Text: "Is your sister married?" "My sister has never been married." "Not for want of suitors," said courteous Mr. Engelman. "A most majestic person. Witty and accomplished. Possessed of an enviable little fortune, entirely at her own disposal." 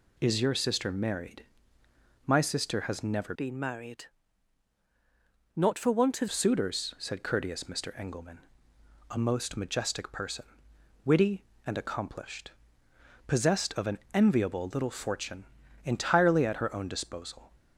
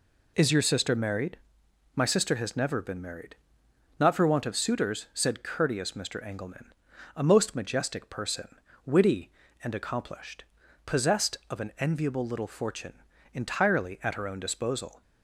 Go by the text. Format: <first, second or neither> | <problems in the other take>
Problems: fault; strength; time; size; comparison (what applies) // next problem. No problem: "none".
second | changes voice from "been" to "of"; from 3.3 to 6.2 s; 2.9 s long // pauses between "an" and "enviable"; slight; at 13.9 s; 0.16 s long